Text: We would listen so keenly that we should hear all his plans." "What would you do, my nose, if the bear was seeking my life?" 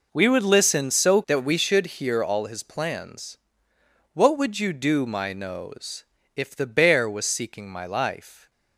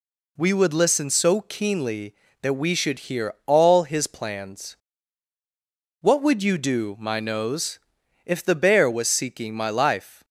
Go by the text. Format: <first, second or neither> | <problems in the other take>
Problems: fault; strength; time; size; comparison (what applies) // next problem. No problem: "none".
second | skips "keenly"; at 1.2 s